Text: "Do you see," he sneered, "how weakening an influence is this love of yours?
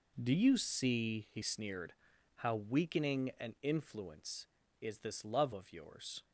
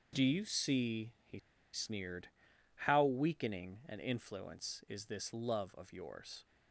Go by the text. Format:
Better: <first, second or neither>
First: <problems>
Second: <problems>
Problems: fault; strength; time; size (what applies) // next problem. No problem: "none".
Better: first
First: none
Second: starts louder than the rest; until 1.2 s; 6.5 dB // pauses between "he" and "sneered"; slight; at 1.3 s; 0.33 s long